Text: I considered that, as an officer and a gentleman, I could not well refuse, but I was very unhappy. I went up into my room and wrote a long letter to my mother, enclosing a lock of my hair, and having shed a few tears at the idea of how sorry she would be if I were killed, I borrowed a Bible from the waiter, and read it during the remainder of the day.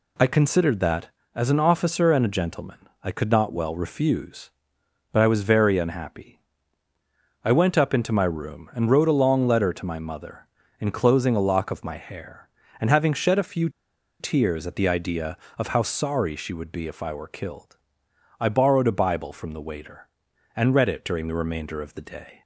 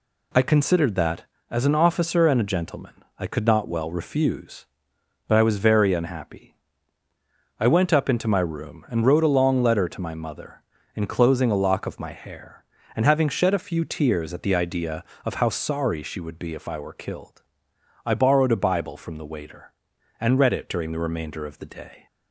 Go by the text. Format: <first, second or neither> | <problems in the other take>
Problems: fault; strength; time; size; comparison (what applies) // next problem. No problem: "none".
second | pauses between "few" and "tears"; noticeable; at 13.6 s; 0.51 s long